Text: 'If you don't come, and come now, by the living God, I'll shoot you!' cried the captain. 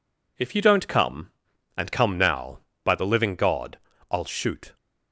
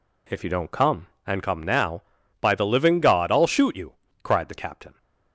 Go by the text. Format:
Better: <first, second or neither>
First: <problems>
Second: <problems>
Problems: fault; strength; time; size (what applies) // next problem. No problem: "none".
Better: second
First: stops before "you cried the captain"; at 4.7 s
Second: none